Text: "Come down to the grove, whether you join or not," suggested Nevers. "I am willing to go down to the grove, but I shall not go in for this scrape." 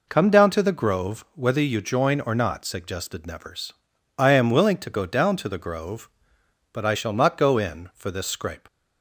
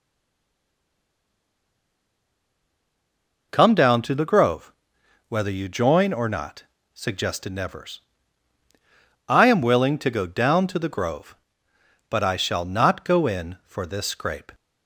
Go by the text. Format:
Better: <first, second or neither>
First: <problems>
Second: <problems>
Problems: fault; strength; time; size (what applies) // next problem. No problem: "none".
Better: first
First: none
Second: stays silent before the first word; strong; until 3.5 s; 3.5 s long